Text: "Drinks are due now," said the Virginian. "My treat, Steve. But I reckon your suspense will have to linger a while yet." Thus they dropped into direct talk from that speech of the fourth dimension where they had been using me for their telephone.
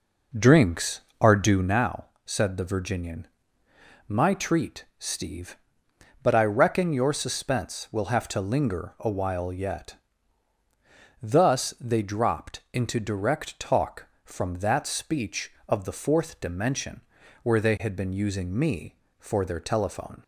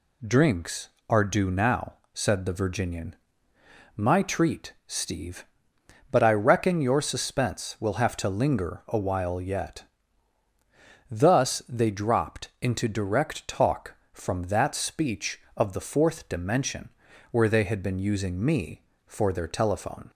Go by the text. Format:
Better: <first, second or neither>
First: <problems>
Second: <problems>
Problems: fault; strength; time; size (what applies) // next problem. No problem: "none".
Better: second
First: starts louder than the rest; noticeable; until 1.8 s; 5 dB // pauses between "dimension" and "where"; at 17.0 s; 0.42 s long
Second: pauses between "dimension" and "where"; at 16.8 s; 0.42 s long